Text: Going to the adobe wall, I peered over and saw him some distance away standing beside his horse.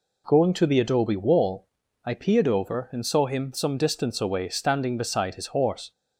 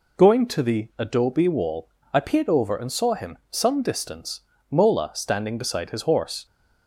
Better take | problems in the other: first | says "mola" for "away"; at 4.6 s

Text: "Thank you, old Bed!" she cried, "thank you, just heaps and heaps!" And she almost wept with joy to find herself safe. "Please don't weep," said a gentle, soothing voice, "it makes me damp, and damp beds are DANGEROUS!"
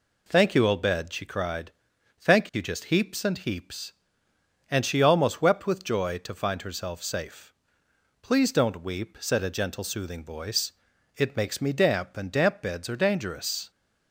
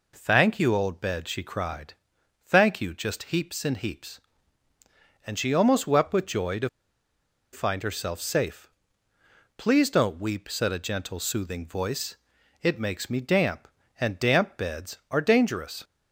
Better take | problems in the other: first | pauses between "to" and "find"; noticeable; at 6.6 s; 0.84 s long

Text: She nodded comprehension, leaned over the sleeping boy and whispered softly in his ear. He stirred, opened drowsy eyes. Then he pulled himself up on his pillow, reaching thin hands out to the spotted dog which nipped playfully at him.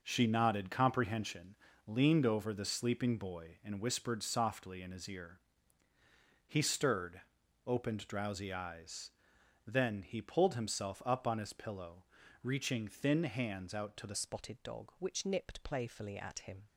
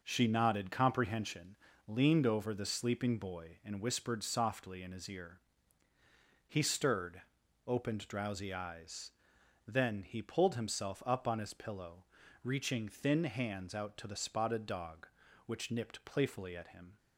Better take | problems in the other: second | changes voice at "spotted"; from 14.1 s on; 2.5 s long

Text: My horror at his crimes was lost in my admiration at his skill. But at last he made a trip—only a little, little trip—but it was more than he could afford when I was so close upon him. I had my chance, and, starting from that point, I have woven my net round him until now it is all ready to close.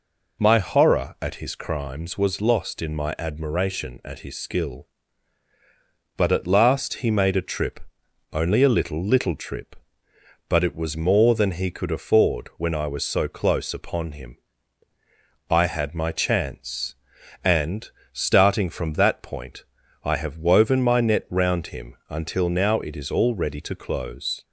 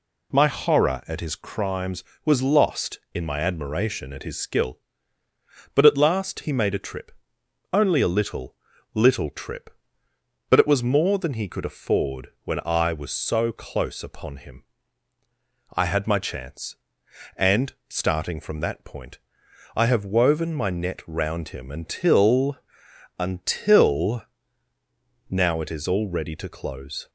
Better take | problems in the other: first | pauses between "afford" and "when"; slight; at 12.2 s; 0.16 s long // says "until" twice; at 23.1 s

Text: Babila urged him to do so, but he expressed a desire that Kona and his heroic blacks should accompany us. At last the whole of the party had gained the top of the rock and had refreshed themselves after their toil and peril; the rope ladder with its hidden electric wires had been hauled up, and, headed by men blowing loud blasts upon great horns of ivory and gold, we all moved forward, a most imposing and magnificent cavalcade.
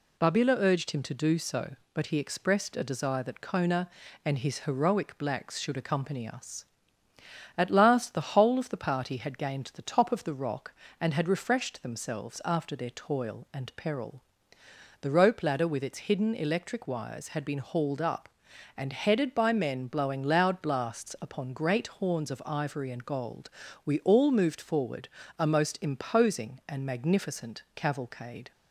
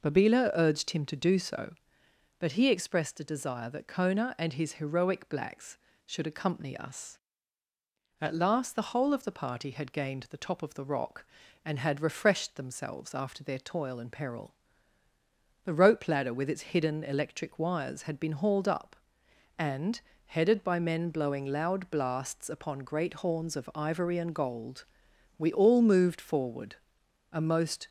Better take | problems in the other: first | stops before "imposing and magnificent cavalcade"; at 27.8 s

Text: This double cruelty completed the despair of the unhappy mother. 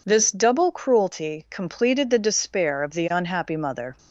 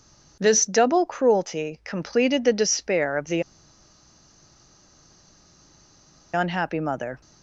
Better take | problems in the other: first | pauses between "the" and "unhappy"; strong; at 3.4 s; 2.9 s long

